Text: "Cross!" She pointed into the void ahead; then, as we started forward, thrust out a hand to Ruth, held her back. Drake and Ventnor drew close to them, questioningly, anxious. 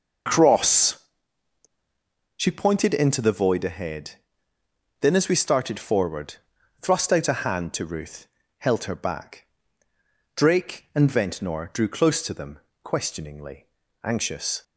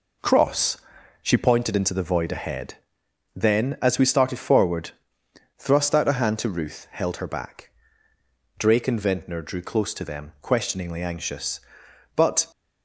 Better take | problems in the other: first | goes on to say "But"; slight; from 12.1 s on; 0.30 s long

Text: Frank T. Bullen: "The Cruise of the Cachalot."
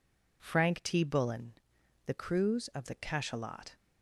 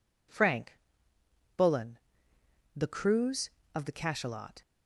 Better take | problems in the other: first | skips "T"; at 1.1 s

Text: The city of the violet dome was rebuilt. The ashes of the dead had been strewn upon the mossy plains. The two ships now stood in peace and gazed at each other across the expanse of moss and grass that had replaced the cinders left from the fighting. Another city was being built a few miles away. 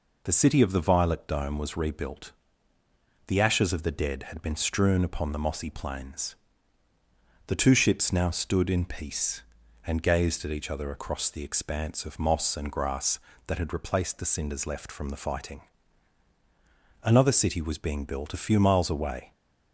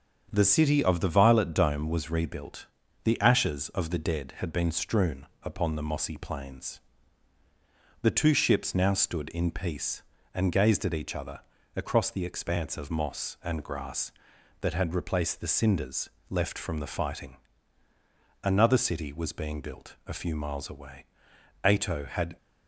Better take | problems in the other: first | starts louder than the rest; strong; until 1.3 s; 7.5 dB // pauses between "strewn" and "upon"; slight; at 5.2 s; 0.16 s long // pauses between "other" and "across"; slight; at 11.3 s; 0.36 s long // pauses between "cinders" and "left"; slight; at 16.1 s; 0.18 s long // goes on to say "Ato had"; noticeable; from 21.6 s on; 0.70 s long

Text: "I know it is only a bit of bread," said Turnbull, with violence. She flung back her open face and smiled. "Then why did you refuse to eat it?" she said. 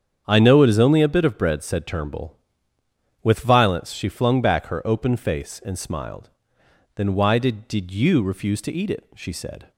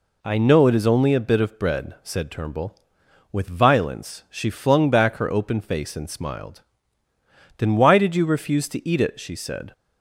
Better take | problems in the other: second | starts louder than the rest; strong; until 1.2 s; 8 dB // says "did" twice; at 7.6 s

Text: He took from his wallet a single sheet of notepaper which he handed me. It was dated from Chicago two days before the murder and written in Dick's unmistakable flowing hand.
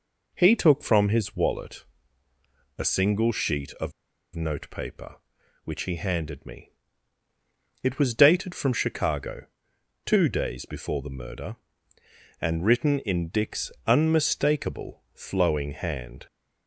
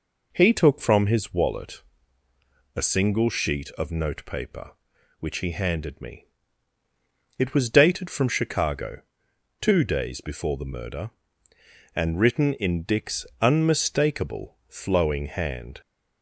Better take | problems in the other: second | pauses between "wallet" and "a"; noticeable; at 1.8 s; 0.94 s long; noticeable in the second // pauses between "of" and "notepaper"; at 3.9 s; 0.44 s long // pauses between "Chicago" and "two"; noticeable; at 9.4 s; 0.58 s long; noticeable in the second // pauses between "Dick's" and "unmistakable"; slight; at 13.7 s; 0.16 s long; slight in the second

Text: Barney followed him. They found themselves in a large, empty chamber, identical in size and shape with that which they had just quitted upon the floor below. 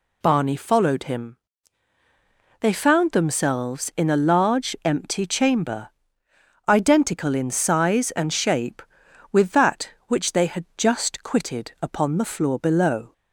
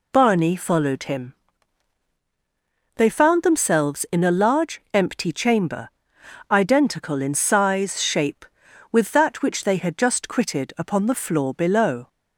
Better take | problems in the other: first | skips "and"; at 8.0 s

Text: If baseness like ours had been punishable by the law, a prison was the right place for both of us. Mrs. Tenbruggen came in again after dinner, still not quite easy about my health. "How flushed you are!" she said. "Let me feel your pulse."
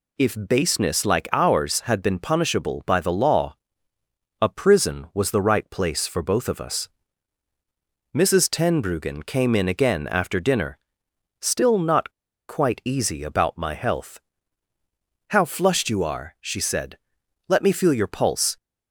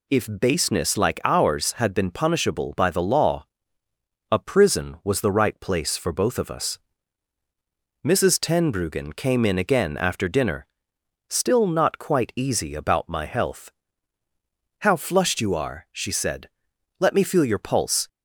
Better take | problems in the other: second | pauses between "not" and "quite"; at 12.1 s; 0.37 s long

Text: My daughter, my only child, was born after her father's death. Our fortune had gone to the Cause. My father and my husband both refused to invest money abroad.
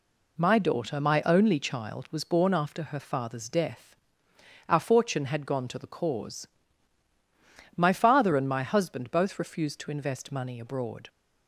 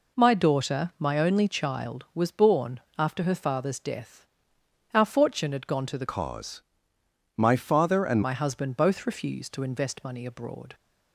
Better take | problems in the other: first | pauses between "born" and "after"; slight; at 2.7 s; 0.18 s long // changes voice from "Cause" to "and"; from 6.0 to 8.2 s; 2.2 s long

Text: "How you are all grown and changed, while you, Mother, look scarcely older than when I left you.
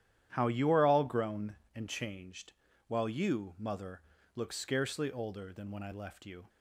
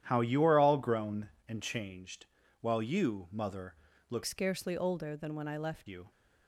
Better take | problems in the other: first | starts louder than the rest; strong; until 1.0 s; 11 dB; strong in the first // changes voice from "scarcely" to "left"; from 4.2 to 5.8 s; 1.6 s long

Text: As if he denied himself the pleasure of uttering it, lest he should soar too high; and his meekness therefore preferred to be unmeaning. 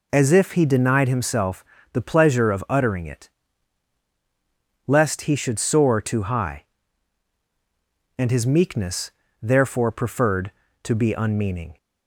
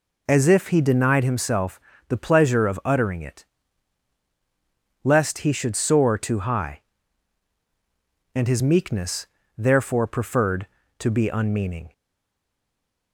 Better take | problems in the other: first | pauses between "himself" and "the"; slight; at 1.7 s; 0.28 s long; slight in the first // pauses between "meekness" and "therefore"; slight; at 9.2 s; 0.32 s long; slight in the first // stays silent after the last word; noticeable; from 11.9 s on; 1.2 s long

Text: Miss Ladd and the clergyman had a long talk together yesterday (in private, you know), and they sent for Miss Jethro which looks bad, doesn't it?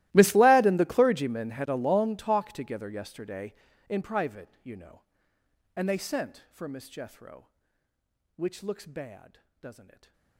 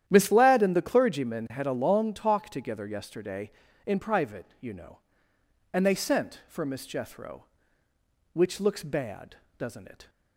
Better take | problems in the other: second | gets quieter; strong; throughout; 25 dB // starts louder than the rest; strong; until 1.1 s; 16.5 dB; strong in the second // stays silent after the last word; slight; from 9.8 s on; 0.5 s long

